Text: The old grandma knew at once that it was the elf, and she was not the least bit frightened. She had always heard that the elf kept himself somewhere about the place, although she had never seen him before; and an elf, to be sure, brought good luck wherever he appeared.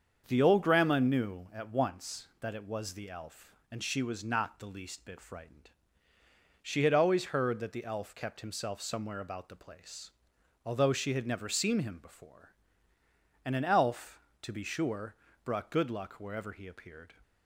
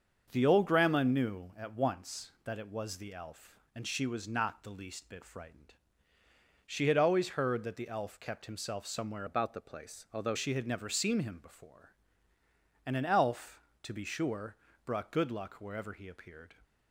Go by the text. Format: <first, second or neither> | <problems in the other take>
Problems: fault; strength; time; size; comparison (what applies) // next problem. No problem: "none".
first | starts louder than the rest; until 1.3 s; 6.5 dB; also in the first // changes voice from "about" to "although"; from 9.2 to 10.3 s; 1.1 s long